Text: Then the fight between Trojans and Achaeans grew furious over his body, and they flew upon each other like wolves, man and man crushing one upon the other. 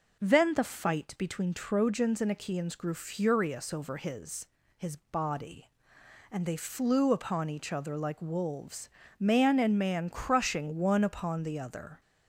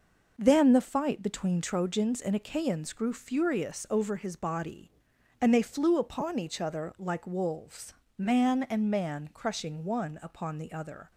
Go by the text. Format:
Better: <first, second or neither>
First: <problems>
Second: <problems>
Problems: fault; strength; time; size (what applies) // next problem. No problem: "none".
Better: second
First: says "his" twice; at 4.7 s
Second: none